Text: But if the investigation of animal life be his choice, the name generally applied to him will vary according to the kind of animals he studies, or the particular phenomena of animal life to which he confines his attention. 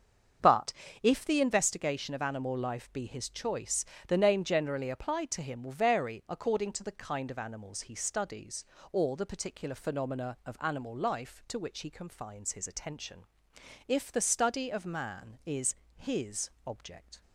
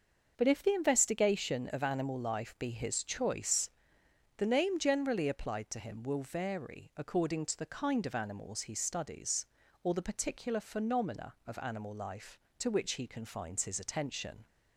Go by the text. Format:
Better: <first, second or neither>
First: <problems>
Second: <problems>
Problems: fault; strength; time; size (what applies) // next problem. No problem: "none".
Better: second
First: starts louder than the rest; until 1.7 s; 7 dB // pauses between "But" and "if"; slight; at 0.7 s; 0.30 s long // goes on to say "If the study of man is his object"; strong; from 13.8 s on; 3.3 s long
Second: starts louder than the rest; until 1.3 s; 6 dB